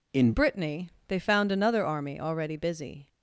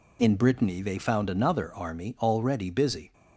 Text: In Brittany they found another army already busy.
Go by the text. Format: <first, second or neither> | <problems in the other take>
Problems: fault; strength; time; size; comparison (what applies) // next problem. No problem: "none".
second | changes voice at "Brittany"; from 0.3 s on; 2.7 s long // pauses between "Brittany" and "they"; slight; at 0.8 s; 0.18 s long